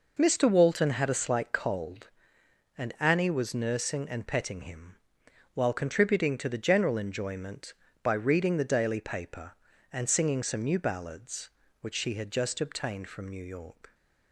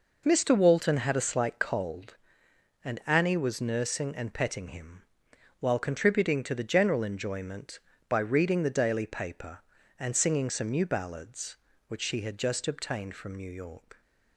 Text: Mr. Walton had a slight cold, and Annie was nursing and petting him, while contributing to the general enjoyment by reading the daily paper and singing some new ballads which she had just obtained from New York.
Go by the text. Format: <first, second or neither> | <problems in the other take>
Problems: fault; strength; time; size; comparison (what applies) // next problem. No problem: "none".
neither | none